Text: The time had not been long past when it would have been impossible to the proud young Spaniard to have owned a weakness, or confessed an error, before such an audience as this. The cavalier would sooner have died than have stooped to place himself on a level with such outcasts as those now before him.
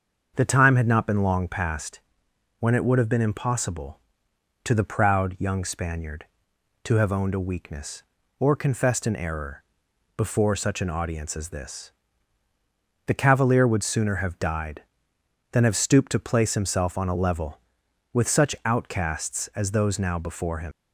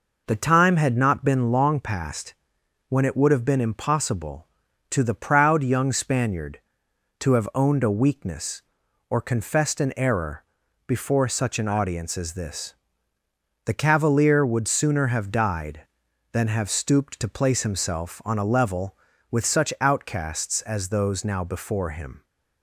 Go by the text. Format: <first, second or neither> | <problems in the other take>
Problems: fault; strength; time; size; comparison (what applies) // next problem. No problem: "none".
second | starts louder than the rest; until 1.3 s; 6.5 dB // pauses between "past" and "when"; noticeable; at 1.9 s; 0.58 s long; noticeable in the second // leaves "him" unfinished; at 20.7 s; 120 ms